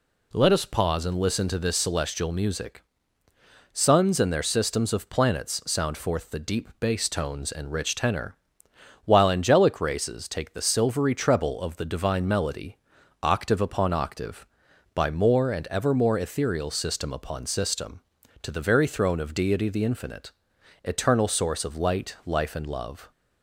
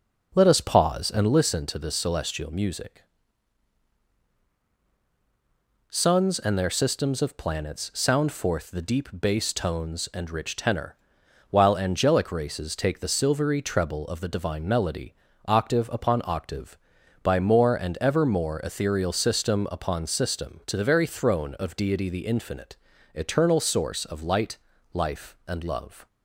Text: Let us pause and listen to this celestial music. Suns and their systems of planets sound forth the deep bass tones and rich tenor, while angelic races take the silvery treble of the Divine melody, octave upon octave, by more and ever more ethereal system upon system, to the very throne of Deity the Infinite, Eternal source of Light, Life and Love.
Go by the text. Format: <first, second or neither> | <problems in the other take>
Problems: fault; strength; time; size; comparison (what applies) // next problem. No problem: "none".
first | starts louder than the rest; noticeable; until 1.4 s; 5.5 dB